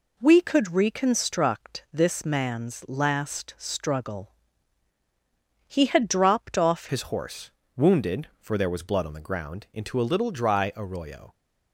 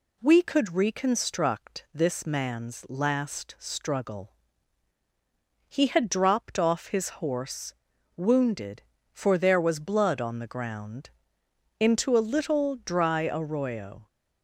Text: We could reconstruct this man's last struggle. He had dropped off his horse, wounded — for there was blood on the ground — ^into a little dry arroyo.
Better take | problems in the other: second | changes voice at "his"; from 6.8 s on; 4.5 s long

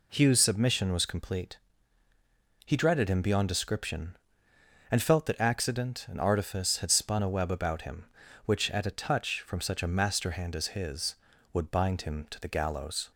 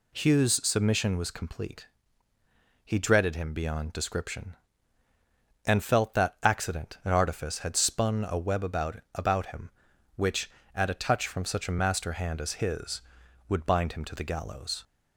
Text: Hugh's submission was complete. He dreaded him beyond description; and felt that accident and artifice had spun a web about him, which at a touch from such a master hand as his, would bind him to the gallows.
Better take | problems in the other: first | says "about" twice; at 9.1 s

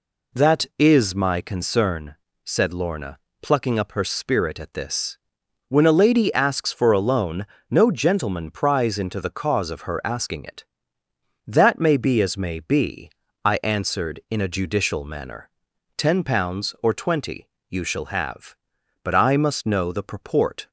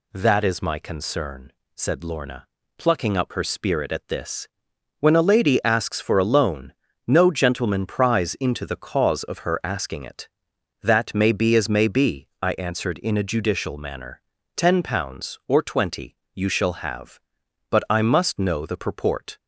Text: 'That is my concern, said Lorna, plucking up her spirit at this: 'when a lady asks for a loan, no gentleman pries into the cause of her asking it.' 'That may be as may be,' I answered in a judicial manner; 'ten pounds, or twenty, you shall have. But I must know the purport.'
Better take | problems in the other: neither | none

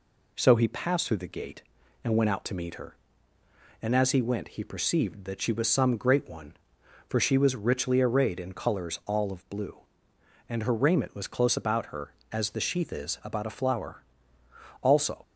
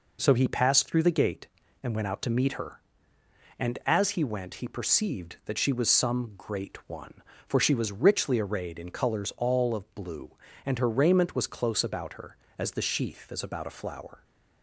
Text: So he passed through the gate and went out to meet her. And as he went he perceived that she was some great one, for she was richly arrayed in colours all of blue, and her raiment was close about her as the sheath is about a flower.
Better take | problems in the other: second | goes on to say "Also"; slight; from 14.8 s on; 0.40 s long

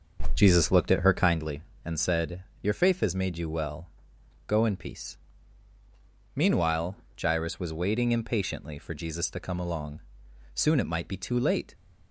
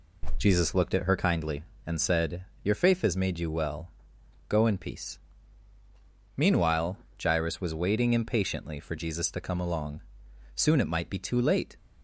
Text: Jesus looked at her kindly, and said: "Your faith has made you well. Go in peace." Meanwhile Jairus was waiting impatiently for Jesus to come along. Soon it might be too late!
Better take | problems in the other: second | starts louder than the rest; until 1.4 s; 6.5 dB // pauses between "Meanwhile" and "Jairus"; slight; at 6.9 s; 0.24 s long; slight in the second

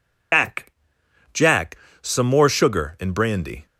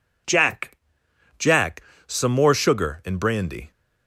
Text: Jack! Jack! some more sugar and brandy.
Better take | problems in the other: second | loses the start of "Jack"; at 0.3 s; 105 ms

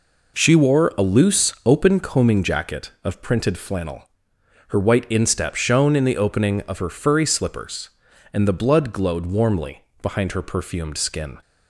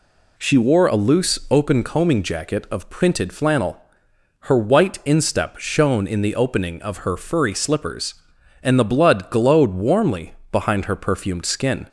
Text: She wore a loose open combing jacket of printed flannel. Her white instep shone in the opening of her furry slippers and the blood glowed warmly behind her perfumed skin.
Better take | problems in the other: neither | pauses between "warmly" and "behind"; slight; the same in both

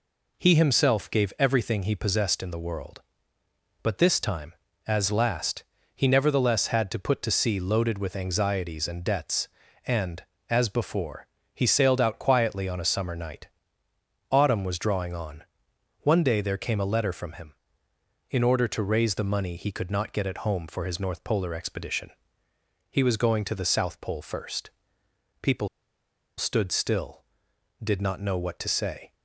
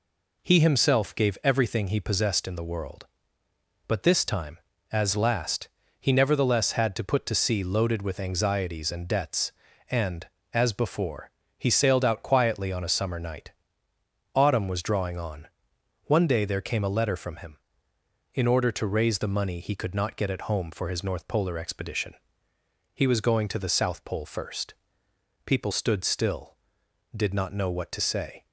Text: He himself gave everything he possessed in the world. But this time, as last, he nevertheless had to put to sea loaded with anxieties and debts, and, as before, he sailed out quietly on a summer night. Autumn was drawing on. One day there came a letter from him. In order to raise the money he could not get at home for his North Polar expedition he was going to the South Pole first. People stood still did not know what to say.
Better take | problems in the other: second | pauses between "expedition" and "he"; noticeable; at 22.1 s; 0.80 s long; noticeable in the second // pauses between "People" and "stood"; noticeable; at 25.6 s; 0.71 s long

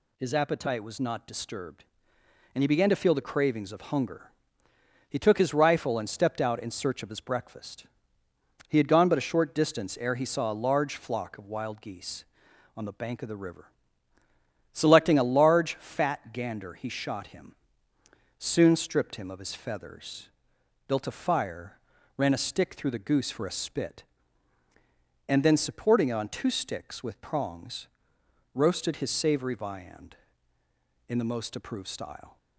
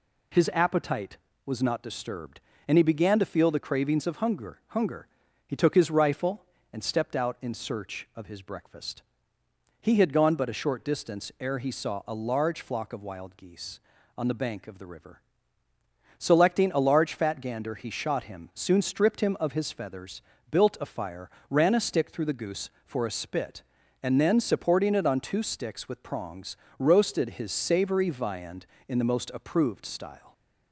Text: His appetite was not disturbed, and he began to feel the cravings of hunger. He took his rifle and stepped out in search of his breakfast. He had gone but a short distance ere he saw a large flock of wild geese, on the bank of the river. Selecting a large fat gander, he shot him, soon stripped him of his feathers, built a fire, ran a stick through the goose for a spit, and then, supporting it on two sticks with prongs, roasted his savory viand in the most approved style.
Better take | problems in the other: first | says "hunger" twice; at 4.6 s

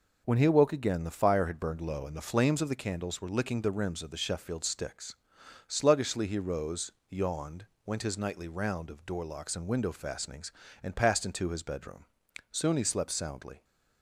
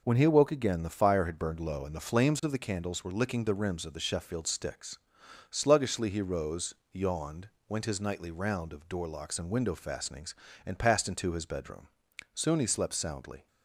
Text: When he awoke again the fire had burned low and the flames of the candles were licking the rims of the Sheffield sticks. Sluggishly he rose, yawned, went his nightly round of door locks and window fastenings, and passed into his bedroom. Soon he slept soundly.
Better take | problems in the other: neither | none

